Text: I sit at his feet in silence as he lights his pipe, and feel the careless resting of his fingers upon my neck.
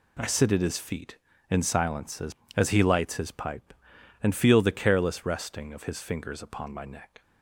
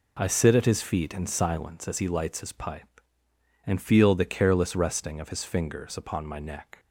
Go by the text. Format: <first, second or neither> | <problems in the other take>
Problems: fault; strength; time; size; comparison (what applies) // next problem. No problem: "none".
second | says "as" twice; at 2.5 s